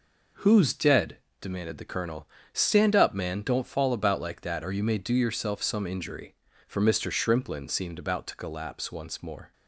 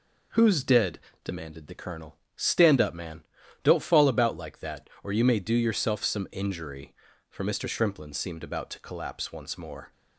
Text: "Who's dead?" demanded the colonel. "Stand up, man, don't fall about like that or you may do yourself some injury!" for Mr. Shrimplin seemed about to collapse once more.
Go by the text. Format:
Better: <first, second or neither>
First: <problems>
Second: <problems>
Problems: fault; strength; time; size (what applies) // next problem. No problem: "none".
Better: neither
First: none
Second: none